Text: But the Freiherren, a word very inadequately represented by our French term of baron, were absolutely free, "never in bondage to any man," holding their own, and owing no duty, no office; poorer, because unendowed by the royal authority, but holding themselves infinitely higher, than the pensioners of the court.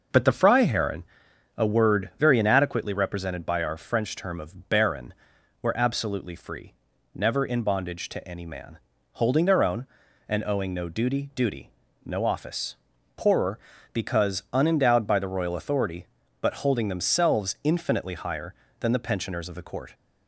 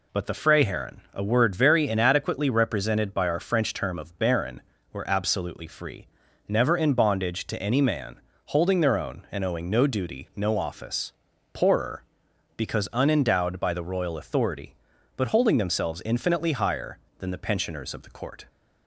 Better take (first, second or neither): second